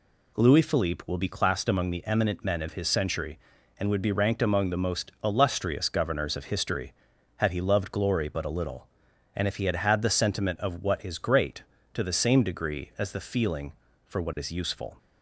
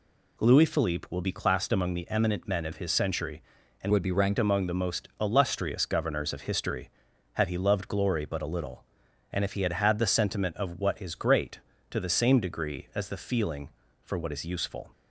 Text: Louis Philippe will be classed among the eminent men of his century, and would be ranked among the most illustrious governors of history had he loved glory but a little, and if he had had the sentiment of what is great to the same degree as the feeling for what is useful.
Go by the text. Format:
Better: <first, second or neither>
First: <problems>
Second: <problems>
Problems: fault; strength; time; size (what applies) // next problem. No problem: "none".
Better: first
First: none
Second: changes voice from "would" to "ranked"; from 3.9 to 4.3 s; 0.4 s long